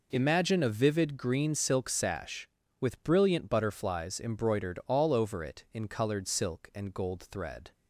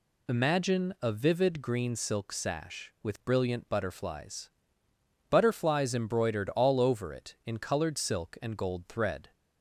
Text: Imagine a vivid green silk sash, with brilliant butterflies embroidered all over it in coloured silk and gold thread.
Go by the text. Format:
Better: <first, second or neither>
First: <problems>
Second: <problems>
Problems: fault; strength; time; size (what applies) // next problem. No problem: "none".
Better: first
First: none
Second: says "butterflies" twice; at 5.3 s